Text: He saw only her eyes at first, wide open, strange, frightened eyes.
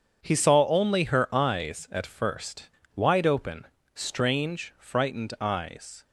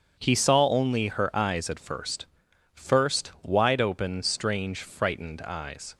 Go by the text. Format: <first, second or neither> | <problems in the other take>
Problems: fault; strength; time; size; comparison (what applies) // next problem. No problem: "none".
first | starts louder than the rest; strong; until 1.2 s; 7 dB; strong in the first // says "first" twice; at 2.7 s